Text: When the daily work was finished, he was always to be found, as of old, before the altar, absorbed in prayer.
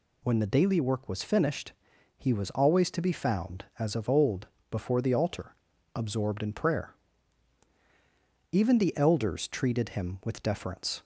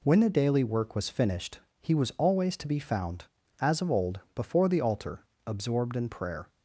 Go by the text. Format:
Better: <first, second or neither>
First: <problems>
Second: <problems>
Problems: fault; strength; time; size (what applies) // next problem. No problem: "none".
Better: second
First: goes on to say "Even the elders treated him with deference"; strong; from 8.5 s on; 2.5 s long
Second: none